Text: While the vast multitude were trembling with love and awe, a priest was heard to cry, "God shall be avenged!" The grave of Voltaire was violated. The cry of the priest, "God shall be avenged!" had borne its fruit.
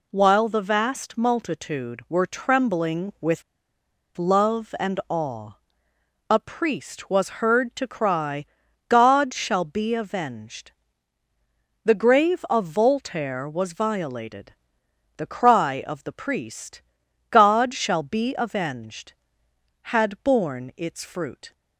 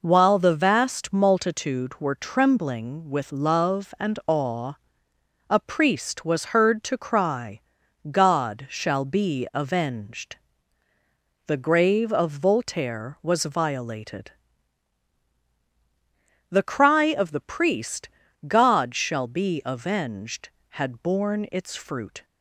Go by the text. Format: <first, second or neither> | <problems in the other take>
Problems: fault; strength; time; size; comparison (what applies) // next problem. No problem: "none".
second | pauses between "with" and "love"; noticeable; at 3.4 s; 0.74 s long